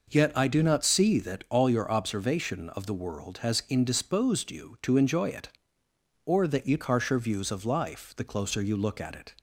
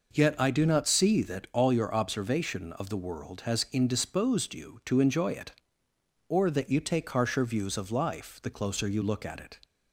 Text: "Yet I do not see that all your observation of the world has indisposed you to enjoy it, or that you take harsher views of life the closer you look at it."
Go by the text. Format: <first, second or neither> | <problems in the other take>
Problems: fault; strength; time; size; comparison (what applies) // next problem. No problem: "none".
second | skips "take"; at 6.8 s